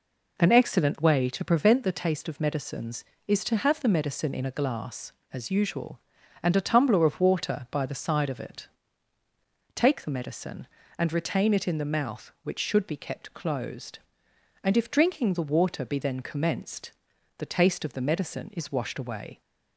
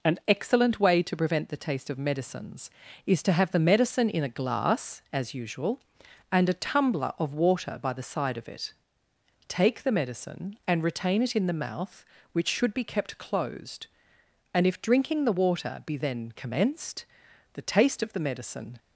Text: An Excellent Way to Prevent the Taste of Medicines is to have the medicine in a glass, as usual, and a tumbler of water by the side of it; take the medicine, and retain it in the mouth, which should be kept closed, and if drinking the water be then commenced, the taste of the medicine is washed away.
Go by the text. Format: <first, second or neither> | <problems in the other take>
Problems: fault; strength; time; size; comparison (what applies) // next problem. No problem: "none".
first | stops before "is washed away"; at 18.7 s